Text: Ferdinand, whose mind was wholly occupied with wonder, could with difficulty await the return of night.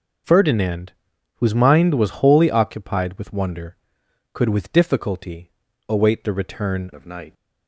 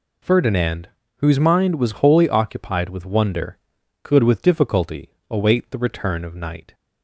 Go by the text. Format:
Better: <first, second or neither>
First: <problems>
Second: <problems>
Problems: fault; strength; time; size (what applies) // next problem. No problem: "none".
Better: second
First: pauses between "difficulty" and "await"; slight; at 5.5 s; 0.36 s long // changes voice at "of"; from 6.9 s on; 0.4 s long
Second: pauses between "difficulty" and "await"; slight; at 5.1 s; 0.18 s long